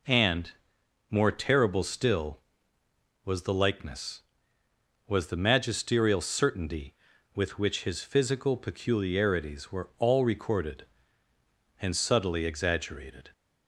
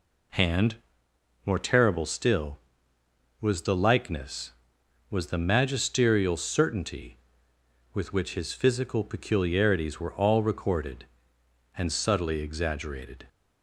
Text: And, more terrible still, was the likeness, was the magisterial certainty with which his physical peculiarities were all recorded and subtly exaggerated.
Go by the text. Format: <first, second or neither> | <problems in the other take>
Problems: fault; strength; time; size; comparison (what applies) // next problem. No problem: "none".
neither | none